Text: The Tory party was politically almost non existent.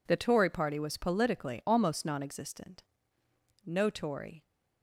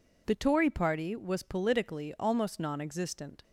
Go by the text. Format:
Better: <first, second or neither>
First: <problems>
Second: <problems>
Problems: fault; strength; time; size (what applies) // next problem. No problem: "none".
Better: second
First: goes on to say "No Tory"; noticeable; from 3.6 s on; 0.82 s long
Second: none